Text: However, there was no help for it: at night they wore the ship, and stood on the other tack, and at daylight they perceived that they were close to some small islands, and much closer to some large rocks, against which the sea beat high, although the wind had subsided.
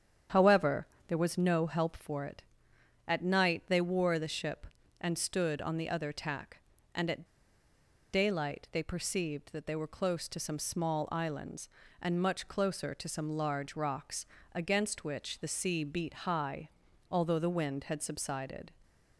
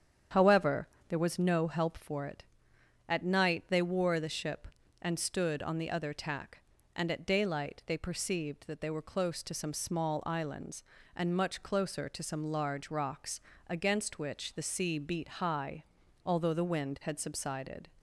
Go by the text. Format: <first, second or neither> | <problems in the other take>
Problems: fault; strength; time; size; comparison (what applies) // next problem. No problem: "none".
second | starts louder than the rest; strong; until 1.5 s; 8.5 dB; strong in the second // pauses between "at" and "daylight"; noticeable; at 7.2 s; 0.88 s long